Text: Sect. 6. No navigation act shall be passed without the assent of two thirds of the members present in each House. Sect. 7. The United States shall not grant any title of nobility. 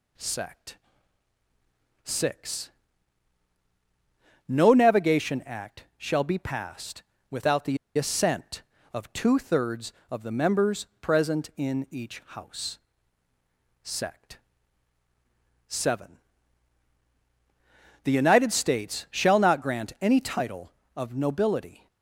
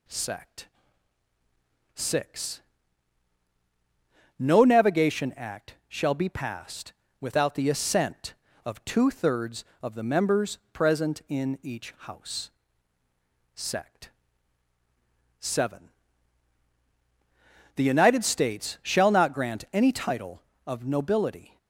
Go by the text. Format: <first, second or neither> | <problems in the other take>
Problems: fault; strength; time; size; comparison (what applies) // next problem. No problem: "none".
second | pauses between "passed" and "without"; slight; at 7.0 s; 0.28 s long; slight in the second // pauses between "the" and "assent"; slight; at 7.7 s; 0.19 s long